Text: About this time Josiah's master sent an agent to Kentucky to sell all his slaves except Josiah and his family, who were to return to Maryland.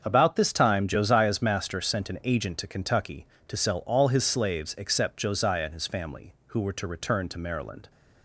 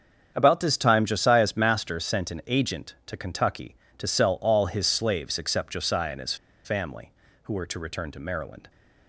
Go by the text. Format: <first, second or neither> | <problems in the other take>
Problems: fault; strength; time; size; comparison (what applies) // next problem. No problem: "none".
first | starts louder than the rest; strong; until 1.3 s; 7.5 dB; also in the first // pauses between "his" and "family"; slight; at 6.3 s; 0.29 s long